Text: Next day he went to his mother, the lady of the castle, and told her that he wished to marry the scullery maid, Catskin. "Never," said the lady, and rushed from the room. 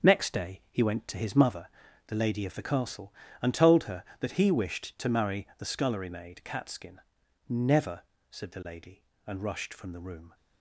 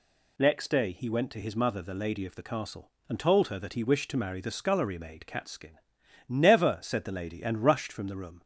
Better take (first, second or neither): second